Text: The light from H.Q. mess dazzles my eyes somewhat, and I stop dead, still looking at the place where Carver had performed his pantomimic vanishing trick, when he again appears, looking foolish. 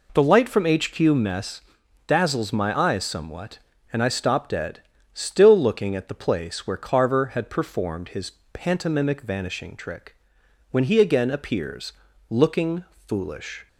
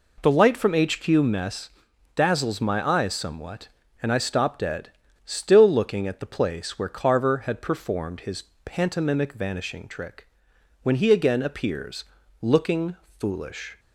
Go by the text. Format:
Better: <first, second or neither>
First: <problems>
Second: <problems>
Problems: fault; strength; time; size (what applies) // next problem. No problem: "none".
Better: neither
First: pauses between "mess" and "dazzles"; noticeable; at 1.6 s; 0.48 s long // pauses between "his" and "pantomimic"; slight; at 8.3 s; 0.20 s long // pauses between "looking" and "foolish"; slight; at 12.8 s; 0.24 s long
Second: pauses between "mess" and "dazzles"; noticeable; at 1.6 s; 0.48 s long // pauses between "his" and "pantomimic"; slight; at 8.4 s; 0.20 s long // pauses between "looking" and "foolish"; slight; at 12.9 s; 0.24 s long